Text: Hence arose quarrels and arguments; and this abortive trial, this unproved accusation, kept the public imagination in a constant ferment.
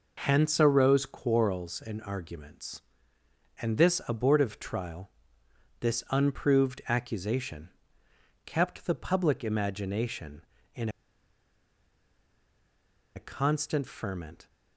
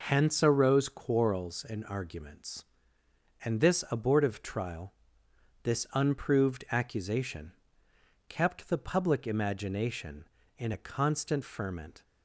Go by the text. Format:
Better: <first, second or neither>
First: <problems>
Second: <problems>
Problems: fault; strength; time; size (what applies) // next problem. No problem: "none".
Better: second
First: pauses between "in" and "a"; strong; at 10.8 s; 2.2 s long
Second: none